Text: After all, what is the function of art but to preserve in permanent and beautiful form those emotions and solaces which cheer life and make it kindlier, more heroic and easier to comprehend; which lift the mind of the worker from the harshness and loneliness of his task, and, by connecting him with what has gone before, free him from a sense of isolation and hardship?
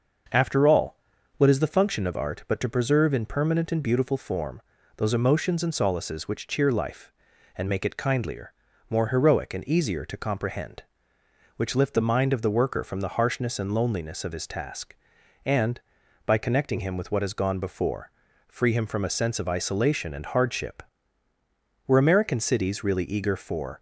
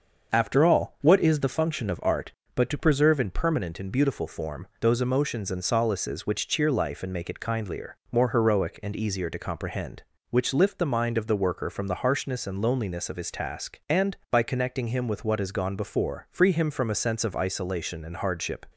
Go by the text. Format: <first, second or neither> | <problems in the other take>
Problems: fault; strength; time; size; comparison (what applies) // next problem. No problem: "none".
second | starts louder than the rest; noticeable; until 1.7 s; 6 dB; also in the second // pauses between "form" and "those"; slight; at 4.6 s; 0.36 s long // goes on to say "Were American cities really eager for"; strong; from 21.8 s on; 1.9 s long